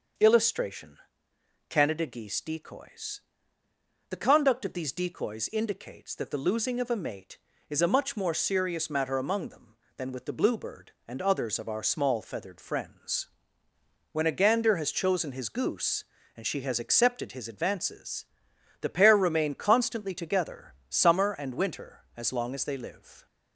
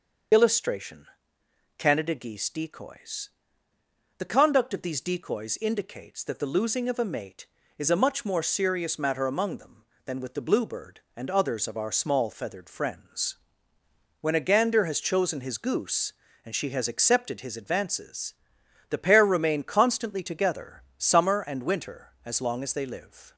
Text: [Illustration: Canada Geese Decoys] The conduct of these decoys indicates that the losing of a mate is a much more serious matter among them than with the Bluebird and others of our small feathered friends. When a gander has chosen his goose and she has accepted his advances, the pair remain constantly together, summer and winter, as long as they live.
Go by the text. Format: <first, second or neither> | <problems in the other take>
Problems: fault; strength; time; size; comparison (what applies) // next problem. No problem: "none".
first | loses the start of "Illustration"; at 0.3 s; 55 ms // starts louder than the rest; until 2.0 s; 6 dB; also in the first // pauses between "Decoys" and "The"; noticeable; at 3.2 s; 0.88 s long; noticeable in the first